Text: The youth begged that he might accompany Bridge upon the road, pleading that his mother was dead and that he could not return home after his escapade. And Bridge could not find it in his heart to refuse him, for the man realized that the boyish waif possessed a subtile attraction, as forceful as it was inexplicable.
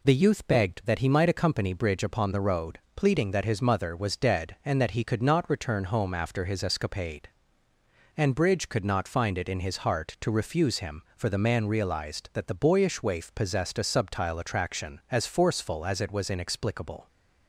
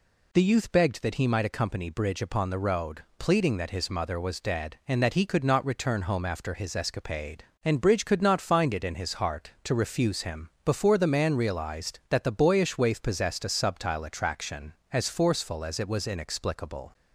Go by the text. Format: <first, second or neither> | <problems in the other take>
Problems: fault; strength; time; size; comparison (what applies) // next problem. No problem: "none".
first | says "before" for "for"; at 10.6 s